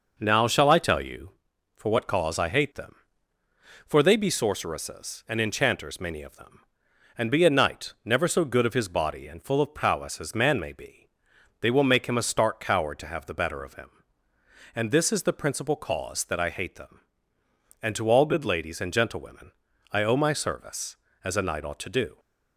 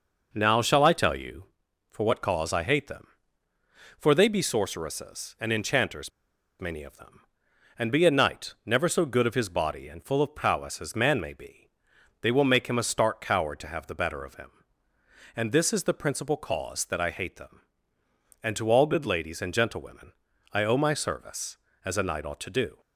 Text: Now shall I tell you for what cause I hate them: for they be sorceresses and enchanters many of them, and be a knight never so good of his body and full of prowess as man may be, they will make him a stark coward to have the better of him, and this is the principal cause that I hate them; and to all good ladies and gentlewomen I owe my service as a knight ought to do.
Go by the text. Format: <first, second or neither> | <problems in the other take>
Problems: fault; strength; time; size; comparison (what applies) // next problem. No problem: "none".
first | pauses between "enchanters" and "many"; noticeable; at 6.1 s; 0.51 s long // pauses between "gentlewomen" and "I"; at 20.1 s; 0.40 s long; also in the first